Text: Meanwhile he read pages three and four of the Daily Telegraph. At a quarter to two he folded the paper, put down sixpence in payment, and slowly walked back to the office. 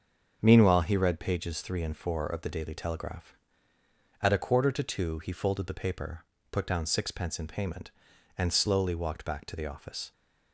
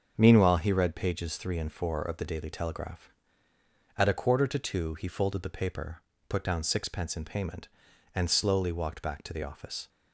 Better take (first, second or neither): neither